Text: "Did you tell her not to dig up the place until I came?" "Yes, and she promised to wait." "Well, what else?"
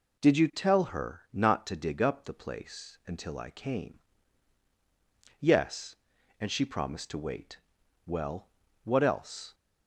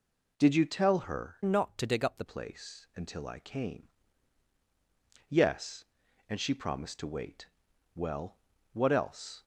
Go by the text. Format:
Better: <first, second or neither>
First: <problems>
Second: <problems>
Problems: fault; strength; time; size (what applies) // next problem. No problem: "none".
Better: first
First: none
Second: changes voice from "not" to "the"; from 1.4 to 2.2 s; 0.8 s long